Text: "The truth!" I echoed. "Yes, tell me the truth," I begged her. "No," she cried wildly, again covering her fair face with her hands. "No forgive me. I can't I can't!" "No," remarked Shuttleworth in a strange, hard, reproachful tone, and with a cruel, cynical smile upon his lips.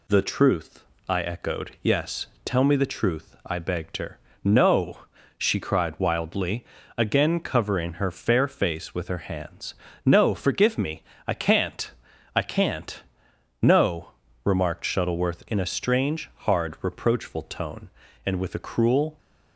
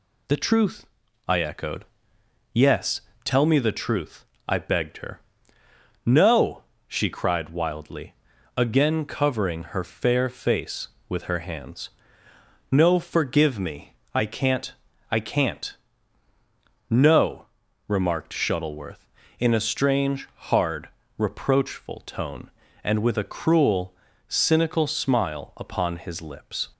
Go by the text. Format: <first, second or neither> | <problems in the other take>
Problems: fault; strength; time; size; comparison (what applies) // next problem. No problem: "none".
second | pauses between "can't" and "I"; noticeable; at 11.8 s; 0.46 s long; also in the second // stops before "cynical smile upon his lips"; at 19.1 s